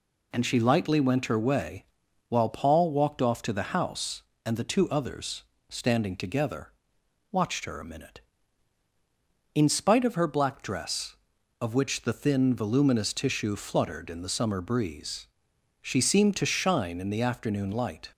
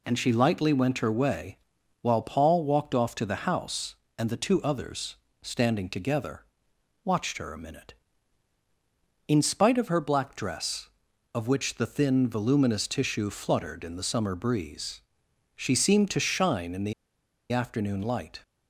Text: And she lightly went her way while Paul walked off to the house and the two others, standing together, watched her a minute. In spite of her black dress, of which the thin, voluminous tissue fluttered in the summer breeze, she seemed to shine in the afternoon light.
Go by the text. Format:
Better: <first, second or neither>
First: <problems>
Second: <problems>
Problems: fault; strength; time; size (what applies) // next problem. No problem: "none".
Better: first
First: pauses between "way" and "while"; at 1.8 s; 0.44 s long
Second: pauses between "way" and "while"; at 1.5 s; 0.44 s long // pauses between "the" and "afternoon"; noticeable; at 16.9 s; 0.58 s long